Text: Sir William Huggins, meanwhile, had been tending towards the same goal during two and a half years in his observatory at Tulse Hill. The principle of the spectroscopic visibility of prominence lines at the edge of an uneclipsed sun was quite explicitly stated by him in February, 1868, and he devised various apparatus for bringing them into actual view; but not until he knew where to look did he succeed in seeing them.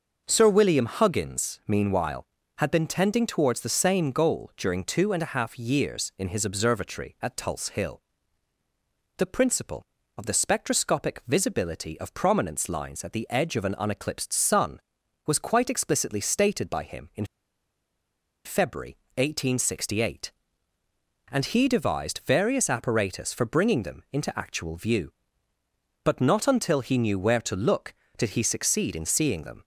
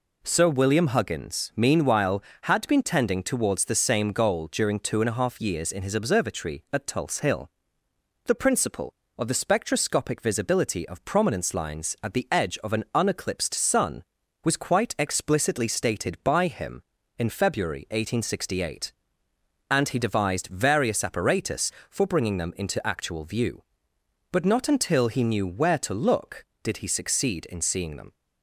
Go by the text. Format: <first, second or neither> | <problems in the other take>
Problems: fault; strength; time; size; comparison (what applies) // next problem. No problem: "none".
second | starts louder than the rest; until 1.2 s; 6 dB // pauses between "in" and "February"; at 17.2 s; 1.1 s long